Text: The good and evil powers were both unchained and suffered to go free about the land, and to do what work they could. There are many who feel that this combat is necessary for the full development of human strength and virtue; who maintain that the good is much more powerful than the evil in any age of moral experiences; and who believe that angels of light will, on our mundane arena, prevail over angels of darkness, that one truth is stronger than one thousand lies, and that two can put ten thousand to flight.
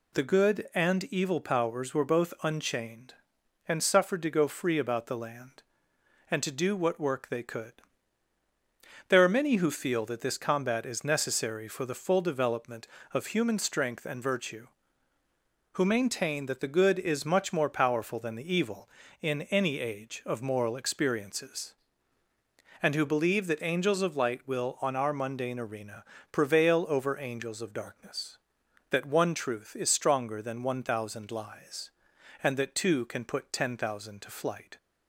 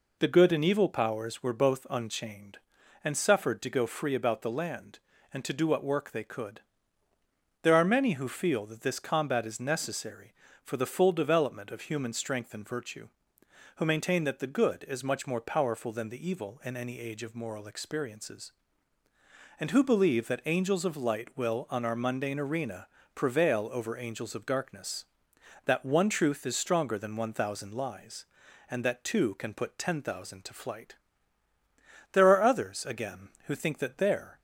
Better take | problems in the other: first | goes on to say "There are others again who think that there"; strong; from 32.1 s on; 2.2 s long

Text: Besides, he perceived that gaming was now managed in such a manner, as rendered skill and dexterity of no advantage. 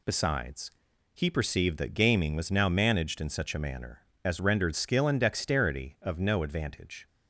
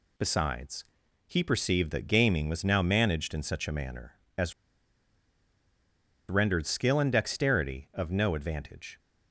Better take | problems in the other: first | pauses between "as" and "rendered"; strong; at 4.5 s; 1.7 s long

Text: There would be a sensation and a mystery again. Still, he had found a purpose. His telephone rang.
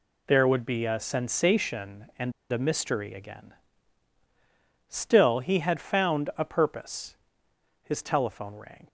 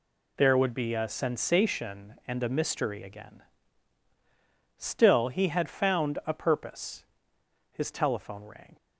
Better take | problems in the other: second | pauses between "and" and "a"; slight; at 2.3 s; 0.19 s long

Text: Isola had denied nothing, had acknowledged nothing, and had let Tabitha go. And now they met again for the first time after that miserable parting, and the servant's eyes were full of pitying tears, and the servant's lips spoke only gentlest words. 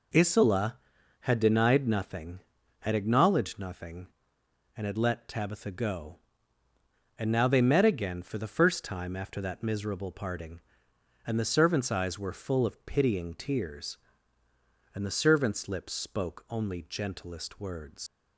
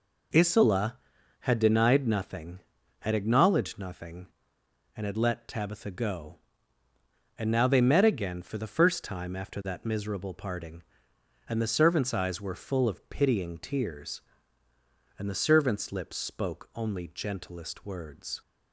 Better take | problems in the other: second | leaves "words" unfinished; at 18.0 s; 90 ms

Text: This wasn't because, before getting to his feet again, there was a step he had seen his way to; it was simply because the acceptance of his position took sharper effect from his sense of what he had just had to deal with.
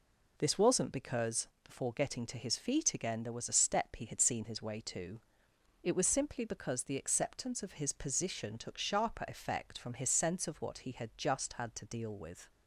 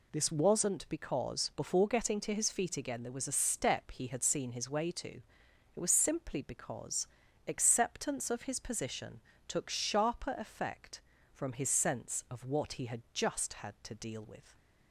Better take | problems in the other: first | skips "the"; at 7.2 s // pauses between "position" and "took"; slight; at 9.1 s; 0.26 s long

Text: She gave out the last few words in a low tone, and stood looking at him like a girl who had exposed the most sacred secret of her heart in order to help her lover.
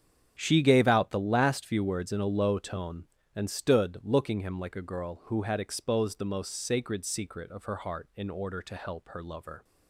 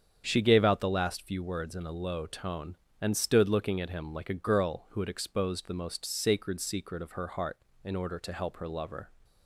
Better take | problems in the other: second | starts louder than the rest; strong; until 1.4 s; 8 dB; strong in the second // skips "at"; at 4.4 s

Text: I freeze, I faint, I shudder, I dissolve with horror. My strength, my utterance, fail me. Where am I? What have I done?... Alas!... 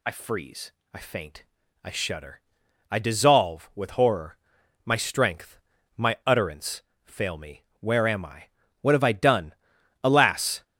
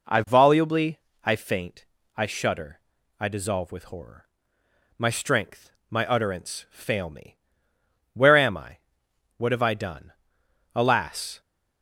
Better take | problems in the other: first | says "volubly" for "freeze"; at 0.2 s

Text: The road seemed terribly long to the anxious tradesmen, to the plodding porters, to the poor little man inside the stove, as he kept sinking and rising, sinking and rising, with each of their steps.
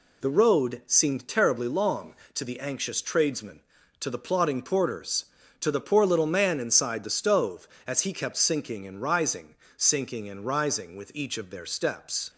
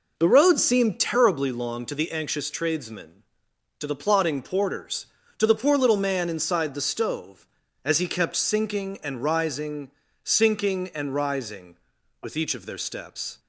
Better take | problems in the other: first | starts louder than the rest; noticeable; until 1.6 s; 4.5 dB

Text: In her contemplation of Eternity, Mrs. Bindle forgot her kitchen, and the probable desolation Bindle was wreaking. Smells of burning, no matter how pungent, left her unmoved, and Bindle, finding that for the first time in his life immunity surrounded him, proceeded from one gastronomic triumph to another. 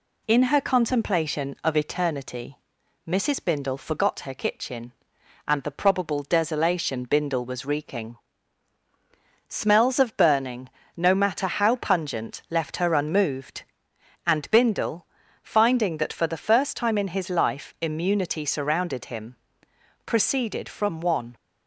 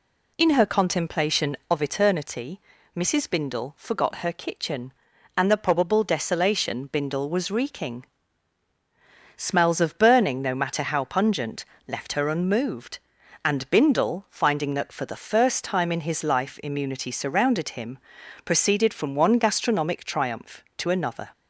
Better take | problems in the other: second | stops before "gastronomic triumph to another"; at 21.3 s

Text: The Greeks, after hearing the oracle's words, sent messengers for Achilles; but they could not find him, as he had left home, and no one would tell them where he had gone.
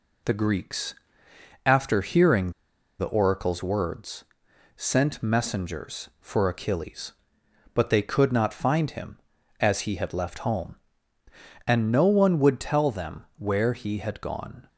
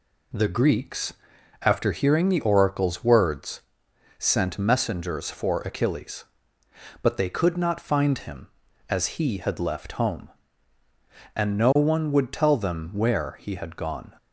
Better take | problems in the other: second | pauses between "hearing" and "the"; noticeable; at 2.5 s; 0.47 s long // pauses between "them" and "where"; slight; at 13.2 s; 0.16 s long

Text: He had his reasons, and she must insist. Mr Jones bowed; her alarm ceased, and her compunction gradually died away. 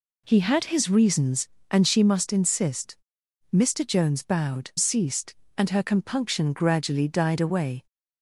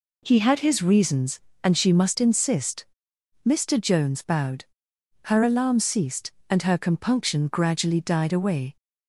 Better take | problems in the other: second | skips "her alarm"; at 4.7 s

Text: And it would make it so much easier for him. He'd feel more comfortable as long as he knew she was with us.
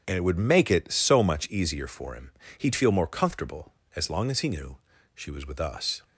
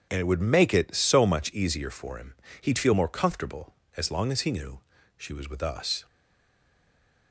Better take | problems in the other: first | starts louder than the rest; strong; until 1.1 s; 7.5 dB; strong in the first // pauses between "knew" and "she"; slight; at 4.7 s; 0.36 s long; slight in the first // stays silent after the last word; noticeable; from 6.0 s on; 1.3 s long

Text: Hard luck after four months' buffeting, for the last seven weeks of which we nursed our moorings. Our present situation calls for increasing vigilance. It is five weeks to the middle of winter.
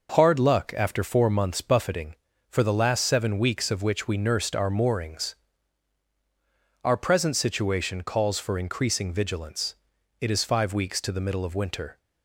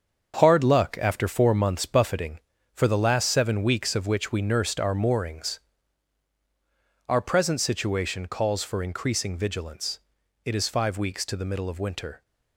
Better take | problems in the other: first | gets quieter; strong; throughout; 8.5 dB

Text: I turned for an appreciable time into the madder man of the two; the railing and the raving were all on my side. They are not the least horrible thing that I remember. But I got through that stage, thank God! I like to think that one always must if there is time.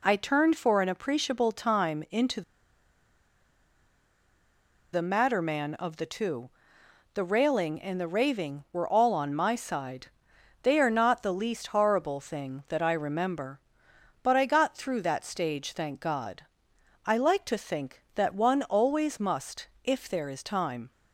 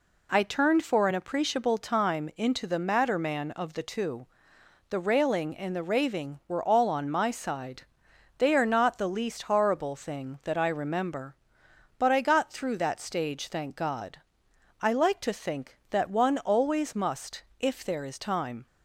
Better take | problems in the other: second | pauses between "into" and "the"; strong; at 2.4 s; 2.5 s long

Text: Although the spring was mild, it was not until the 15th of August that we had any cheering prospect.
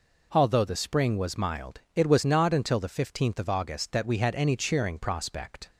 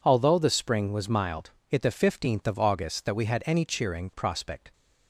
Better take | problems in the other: first | skips "was not until"; at 1.8 s

